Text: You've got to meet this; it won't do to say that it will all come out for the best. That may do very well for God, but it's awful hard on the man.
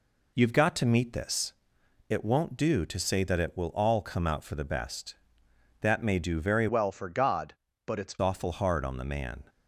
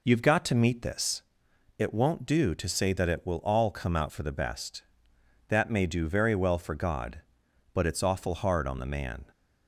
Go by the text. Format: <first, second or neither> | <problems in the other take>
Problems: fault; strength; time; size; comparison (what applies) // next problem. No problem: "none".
second | changes voice from "well" to "it's"; from 6.6 to 8.1 s; 1.5 s long